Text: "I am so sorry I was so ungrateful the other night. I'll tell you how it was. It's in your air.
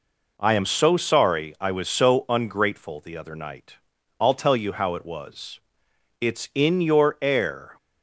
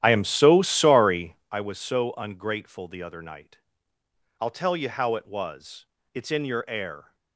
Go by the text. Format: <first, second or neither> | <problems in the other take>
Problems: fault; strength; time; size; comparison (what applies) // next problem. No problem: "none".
first | starts louder than the rest; strong; until 1.6 s; 11.5 dB // pauses between "sorry" and "I"; slight; at 1.3 s; 0.15 s long